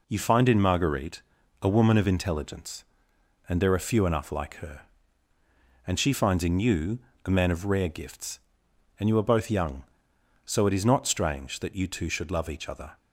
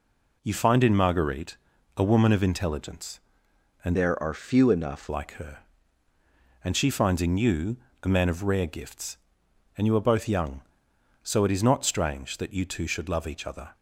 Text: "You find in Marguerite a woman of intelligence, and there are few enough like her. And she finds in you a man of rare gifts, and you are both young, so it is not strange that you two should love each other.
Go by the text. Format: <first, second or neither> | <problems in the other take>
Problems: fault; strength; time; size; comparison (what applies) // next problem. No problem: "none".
first | pauses between "Marguerite" and "a"; at 1.5 s; 0.40 s long; also in the first // changes voice from "there" to "enough"; from 3.9 to 5.0 s; 1.1 s long // pauses between "you" and "a"; slight; at 7.7 s; 0.26 s long; slight in the first